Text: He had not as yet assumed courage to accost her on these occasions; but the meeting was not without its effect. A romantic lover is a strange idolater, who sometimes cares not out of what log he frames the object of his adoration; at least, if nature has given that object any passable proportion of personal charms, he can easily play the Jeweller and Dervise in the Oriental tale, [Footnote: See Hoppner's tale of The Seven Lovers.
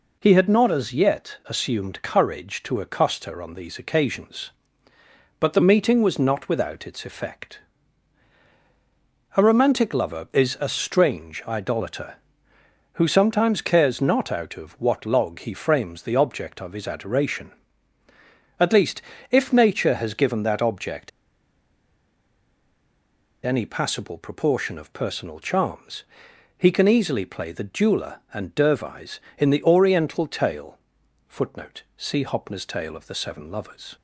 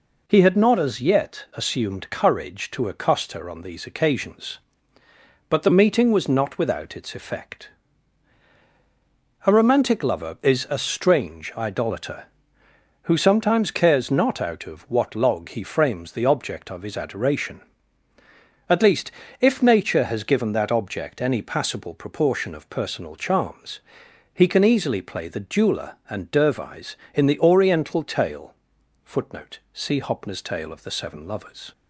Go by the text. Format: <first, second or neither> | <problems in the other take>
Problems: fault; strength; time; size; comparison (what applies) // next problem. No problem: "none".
second | pauses between "object" and "any"; strong; at 21.0 s; 2.3 s long